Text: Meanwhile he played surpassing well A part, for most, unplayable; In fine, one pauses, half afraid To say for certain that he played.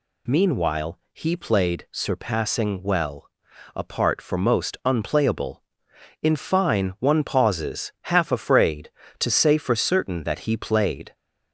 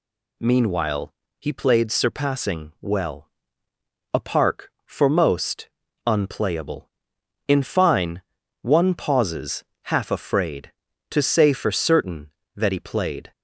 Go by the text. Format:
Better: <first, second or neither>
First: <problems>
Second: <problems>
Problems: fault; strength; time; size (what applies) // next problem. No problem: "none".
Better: first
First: pauses between "well" and "A"; noticeable; at 3.2 s; 0.50 s long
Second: pauses between "Meanwhile" and "he"; slight; at 1.1 s; 0.28 s long // pauses between "well" and "A"; noticeable; at 3.2 s; 0.86 s long // says "park" for "part"; at 4.1 s